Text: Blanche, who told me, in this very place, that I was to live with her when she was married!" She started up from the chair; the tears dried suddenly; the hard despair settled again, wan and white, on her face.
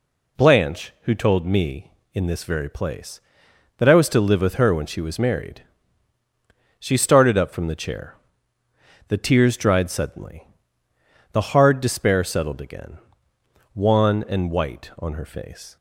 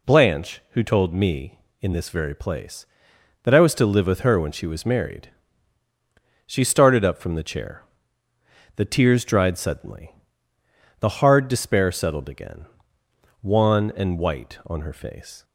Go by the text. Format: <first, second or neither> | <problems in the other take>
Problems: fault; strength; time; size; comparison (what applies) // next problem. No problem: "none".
neither | none